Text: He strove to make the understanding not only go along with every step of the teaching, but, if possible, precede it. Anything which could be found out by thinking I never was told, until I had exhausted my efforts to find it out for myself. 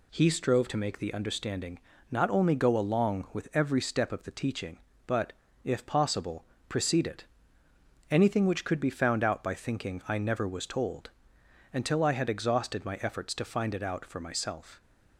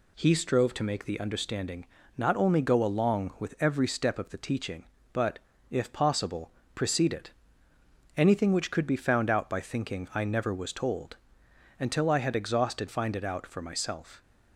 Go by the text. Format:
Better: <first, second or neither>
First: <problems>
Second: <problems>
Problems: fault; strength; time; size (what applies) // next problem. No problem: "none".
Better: first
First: pauses between "understanding" and "not"; slight; at 1.7 s; 0.32 s long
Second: pauses between "understanding" and "not"; slight; at 1.8 s; 0.32 s long // skips "my efforts to"; at 12.8 s